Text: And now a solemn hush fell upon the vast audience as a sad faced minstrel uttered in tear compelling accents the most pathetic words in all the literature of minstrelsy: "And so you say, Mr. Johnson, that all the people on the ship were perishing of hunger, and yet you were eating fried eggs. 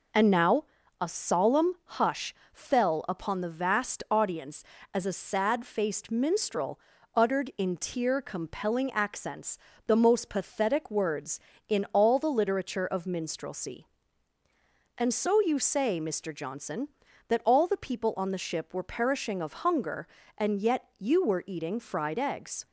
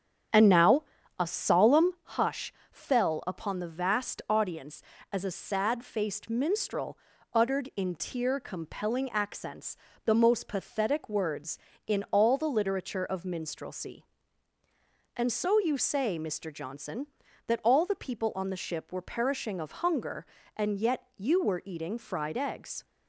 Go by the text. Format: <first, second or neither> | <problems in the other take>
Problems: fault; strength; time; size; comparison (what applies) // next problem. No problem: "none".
first | starts louder than the rest; strong; until 2.1 s; 9 dB // pauses between "now" and "a"; slight; at 0.8 s; 0.36 s long; slight in the first // pauses between "hush" and "fell"; slight; at 2.5 s; 0.18 s long; slight in the first // pauses between "minstrel" and "uttered"; slight; at 6.9 s; 0.34 s long; slight in the first // pauses between "accents" and "the"; slight; at 9.7 s; 0.28 s long; slight in the first